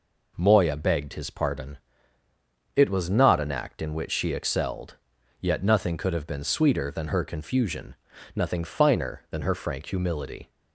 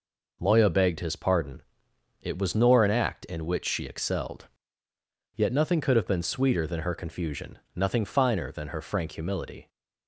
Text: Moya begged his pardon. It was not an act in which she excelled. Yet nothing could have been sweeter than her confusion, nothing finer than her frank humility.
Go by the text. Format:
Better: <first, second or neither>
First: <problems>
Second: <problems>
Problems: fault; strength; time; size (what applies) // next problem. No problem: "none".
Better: first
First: none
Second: says "nor" for "not"; at 2.5 s